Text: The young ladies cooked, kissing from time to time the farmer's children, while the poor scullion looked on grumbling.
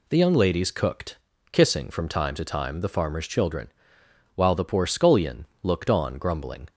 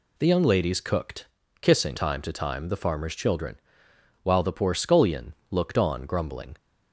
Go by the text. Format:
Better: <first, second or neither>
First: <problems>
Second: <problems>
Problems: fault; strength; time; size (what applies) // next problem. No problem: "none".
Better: first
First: pauses between "scullion" and "looked"; slight; at 5.4 s; 0.16 s long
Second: skips "from"; at 1.9 s // pauses between "scullion" and "looked"; slight; at 5.3 s; 0.16 s long